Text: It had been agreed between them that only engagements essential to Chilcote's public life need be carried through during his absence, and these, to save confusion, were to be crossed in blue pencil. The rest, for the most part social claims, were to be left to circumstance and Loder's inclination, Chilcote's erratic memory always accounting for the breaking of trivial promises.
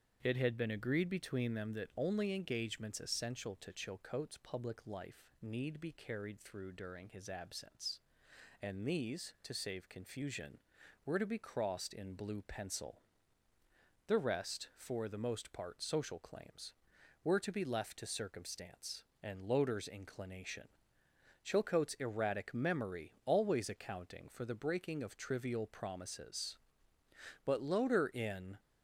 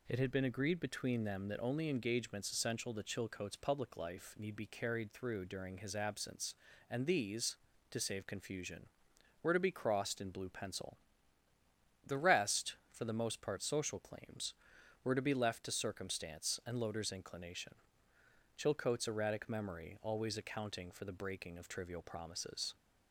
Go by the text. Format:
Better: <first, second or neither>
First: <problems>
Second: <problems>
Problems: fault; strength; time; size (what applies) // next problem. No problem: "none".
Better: second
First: starts louder than the rest; strong; until 1.2 s; 7.5 dB // goes on to say "But Loder in"; noticeable; from 27.4 s on; 1.1 s long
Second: none